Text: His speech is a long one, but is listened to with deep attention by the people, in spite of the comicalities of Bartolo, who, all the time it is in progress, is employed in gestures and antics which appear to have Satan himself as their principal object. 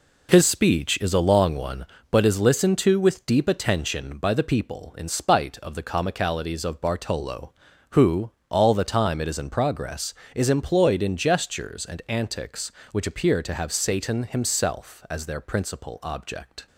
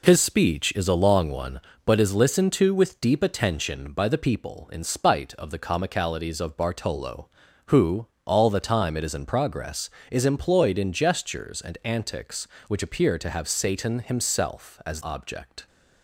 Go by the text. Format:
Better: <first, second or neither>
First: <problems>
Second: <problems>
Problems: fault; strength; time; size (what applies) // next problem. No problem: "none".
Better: first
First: none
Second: skips "their principal"; at 15.0 s